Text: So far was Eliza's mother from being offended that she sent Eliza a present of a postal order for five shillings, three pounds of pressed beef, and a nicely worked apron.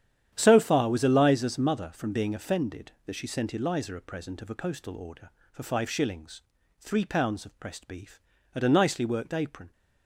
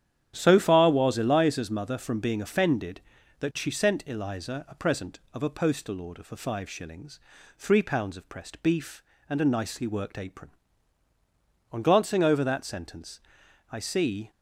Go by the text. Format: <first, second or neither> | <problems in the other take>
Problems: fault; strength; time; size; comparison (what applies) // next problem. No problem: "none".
first | starts louder than the rest; strong; until 1.3 s; 10 dB; strong in the first // goes on to say "On glancing over that sentence I see"; strong; from 11.7 s on; 2.5 s long